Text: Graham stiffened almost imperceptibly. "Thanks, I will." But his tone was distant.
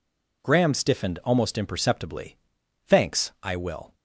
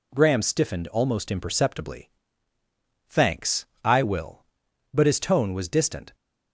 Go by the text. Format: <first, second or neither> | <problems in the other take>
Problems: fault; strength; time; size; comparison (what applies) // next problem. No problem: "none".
second | stops before "But his tone was distant"; at 3.9 s